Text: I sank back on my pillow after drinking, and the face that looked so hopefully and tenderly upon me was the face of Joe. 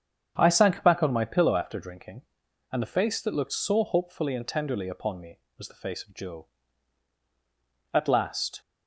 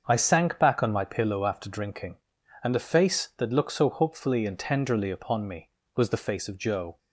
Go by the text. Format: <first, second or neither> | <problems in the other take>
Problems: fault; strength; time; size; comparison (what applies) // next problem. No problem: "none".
second | starts louder than the rest; strong; until 1.3 s; 8 dB; also in the second // goes on to say "At last"; noticeable; from 7.9 s on; 0.66 s long